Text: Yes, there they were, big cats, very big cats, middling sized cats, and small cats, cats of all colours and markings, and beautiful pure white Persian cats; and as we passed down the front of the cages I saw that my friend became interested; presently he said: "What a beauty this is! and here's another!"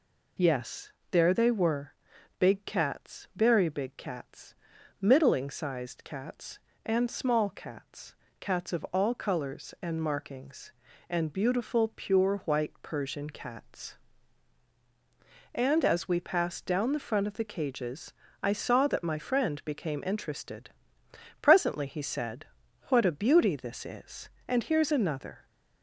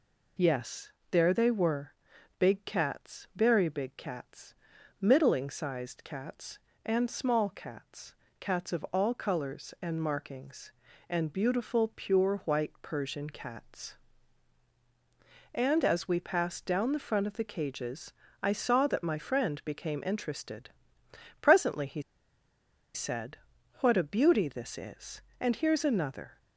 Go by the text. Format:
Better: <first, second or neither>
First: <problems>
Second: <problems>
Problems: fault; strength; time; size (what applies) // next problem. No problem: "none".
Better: first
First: pauses between "cages" and "I"; slight; at 18.1 s; 0.26 s long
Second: pauses between "cages" and "I"; slight; at 18.1 s; 0.26 s long // pauses between "he" and "said"; noticeable; at 22.0 s; 0.93 s long